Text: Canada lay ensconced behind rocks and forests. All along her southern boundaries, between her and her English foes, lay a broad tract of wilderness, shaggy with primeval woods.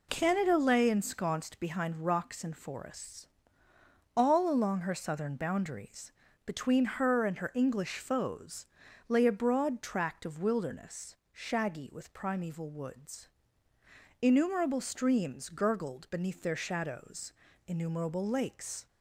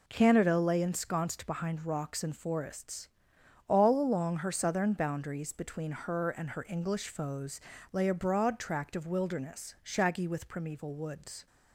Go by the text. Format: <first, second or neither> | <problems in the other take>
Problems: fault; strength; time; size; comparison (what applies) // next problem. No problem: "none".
second | goes on to say "Innumerable streams gurgled beneath their shadows innumerable lakes"; strong; from 14.1 s on; 4.6 s long